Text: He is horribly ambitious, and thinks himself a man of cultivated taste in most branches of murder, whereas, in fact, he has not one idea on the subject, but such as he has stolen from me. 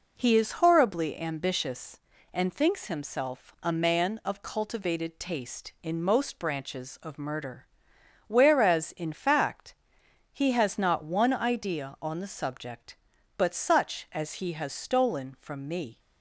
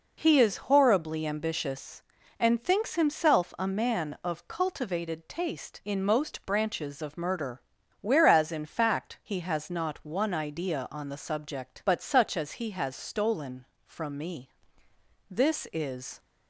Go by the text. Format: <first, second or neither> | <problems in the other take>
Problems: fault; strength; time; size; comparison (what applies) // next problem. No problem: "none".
first | goes on to say "This is"; noticeable; from 15.2 s on; 0.90 s long